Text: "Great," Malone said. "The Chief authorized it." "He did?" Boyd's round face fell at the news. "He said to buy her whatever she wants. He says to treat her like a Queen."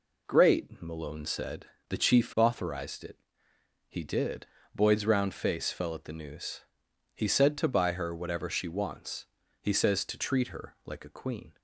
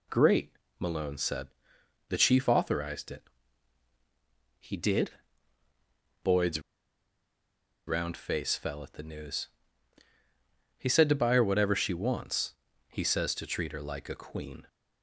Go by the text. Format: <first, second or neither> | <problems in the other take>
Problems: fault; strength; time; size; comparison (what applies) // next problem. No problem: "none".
first | pauses between "Boyd's" and "round"; strong; at 6.6 s; 1.2 s long